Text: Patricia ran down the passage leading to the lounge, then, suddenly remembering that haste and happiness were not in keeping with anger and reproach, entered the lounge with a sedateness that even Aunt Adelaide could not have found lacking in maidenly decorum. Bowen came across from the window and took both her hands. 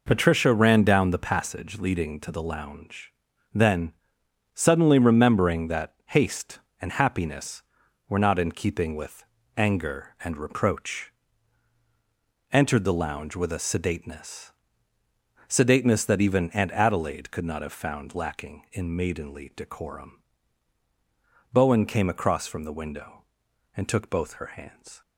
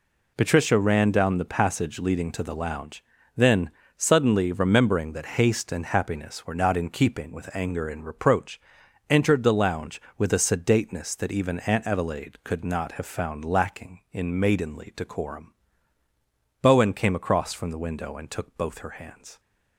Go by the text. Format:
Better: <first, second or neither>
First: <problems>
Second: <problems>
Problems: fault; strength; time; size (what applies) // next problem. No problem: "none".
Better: second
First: pauses between "with" and "anger"; slight; at 9.2 s; 0.32 s long // says "sedateness" twice; at 15.4 s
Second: none